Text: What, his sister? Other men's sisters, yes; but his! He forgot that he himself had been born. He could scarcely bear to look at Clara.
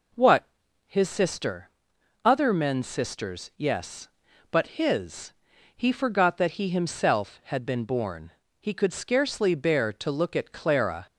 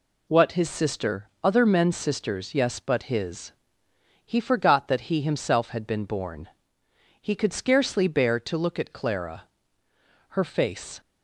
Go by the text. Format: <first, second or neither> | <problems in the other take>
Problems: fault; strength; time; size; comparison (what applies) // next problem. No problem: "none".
first | goes on to say "Her face"; noticeable; from 10.3 s on; 0.70 s long